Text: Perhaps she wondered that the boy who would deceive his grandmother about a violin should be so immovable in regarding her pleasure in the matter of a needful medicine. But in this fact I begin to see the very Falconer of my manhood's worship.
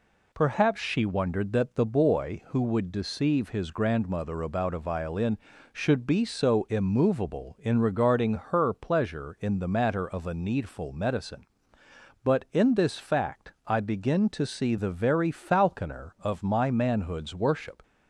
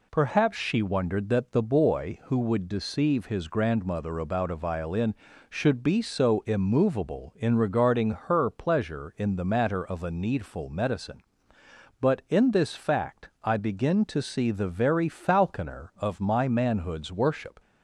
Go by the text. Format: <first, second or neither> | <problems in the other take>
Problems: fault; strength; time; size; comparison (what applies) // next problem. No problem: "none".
neither | none